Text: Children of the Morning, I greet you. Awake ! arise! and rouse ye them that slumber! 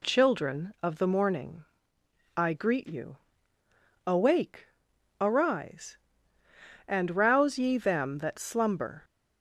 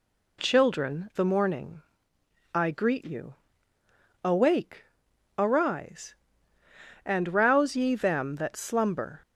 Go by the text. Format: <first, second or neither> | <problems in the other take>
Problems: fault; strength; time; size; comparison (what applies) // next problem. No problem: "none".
first | skips "of"; at 1.1 s